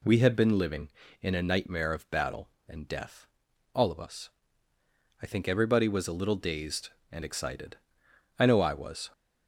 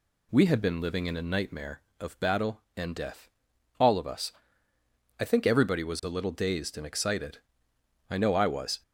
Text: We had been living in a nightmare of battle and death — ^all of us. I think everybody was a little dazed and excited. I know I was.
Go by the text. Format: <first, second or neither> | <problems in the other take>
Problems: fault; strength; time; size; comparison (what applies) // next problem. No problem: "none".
neither | none